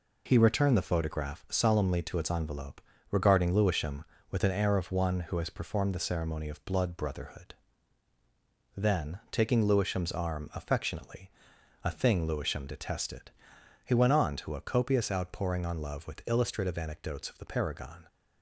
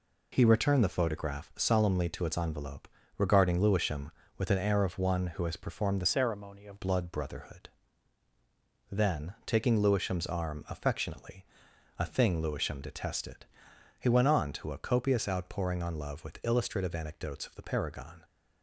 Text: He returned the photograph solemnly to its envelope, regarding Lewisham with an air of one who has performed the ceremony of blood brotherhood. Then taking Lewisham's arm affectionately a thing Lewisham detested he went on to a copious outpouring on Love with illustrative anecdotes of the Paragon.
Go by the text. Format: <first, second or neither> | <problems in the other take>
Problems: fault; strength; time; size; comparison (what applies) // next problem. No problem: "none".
first | changes voice from "ceremony" to "of"; from 6.0 to 6.8 s; 0.8 s long // pauses between "affectionately" and "a"; noticeable; at 11.4 s; 0.54 s long; noticeable in the first // pauses between "detested" and "he"; noticeable; at 13.4 s; 0.54 s long; noticeable in the first